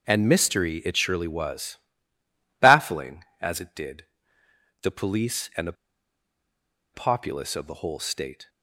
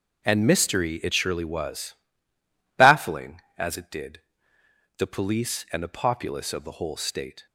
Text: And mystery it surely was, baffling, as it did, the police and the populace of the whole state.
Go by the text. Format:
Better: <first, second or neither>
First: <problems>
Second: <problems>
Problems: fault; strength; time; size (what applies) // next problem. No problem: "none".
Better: second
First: starts louder than the rest; until 1.1 s; 6.5 dB // pauses between "the" and "populace"; at 5.7 s; 1.2 s long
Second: starts louder than the rest; until 1.3 s; 6.5 dB